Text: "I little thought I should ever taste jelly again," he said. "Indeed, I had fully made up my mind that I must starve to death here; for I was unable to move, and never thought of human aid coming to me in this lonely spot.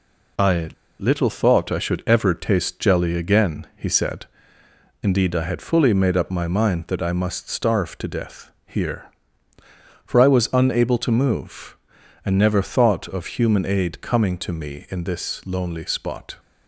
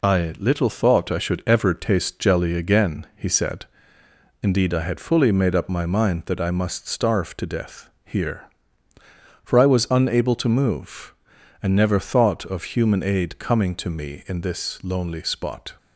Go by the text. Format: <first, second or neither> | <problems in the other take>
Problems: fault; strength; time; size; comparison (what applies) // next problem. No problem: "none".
second | pauses between "I" and "little"; slight; at 0.6 s; 0.29 s long // pauses between "death" and "here"; slight; at 8.5 s; 0.16 s long; slight in the second